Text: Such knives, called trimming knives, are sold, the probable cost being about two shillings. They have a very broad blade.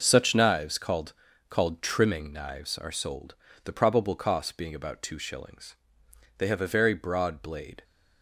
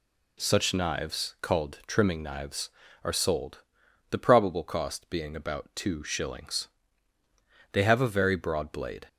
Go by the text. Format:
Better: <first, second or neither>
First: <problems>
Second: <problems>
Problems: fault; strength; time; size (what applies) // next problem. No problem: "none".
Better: second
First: says "called" twice; at 1.4 s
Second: none